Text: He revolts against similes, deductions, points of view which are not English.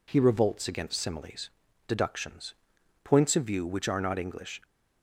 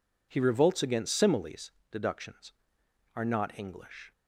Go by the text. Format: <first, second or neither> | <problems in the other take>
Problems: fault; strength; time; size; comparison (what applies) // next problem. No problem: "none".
first | skips "points of view which"; at 2.8 s